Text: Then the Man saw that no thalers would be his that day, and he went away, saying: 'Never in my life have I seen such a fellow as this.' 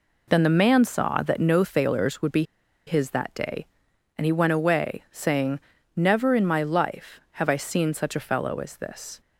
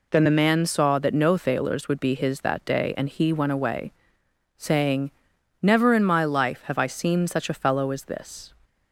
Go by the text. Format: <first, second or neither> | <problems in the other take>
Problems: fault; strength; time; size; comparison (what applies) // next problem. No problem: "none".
second | pauses between "be" and "his"; at 2.4 s; 0.44 s long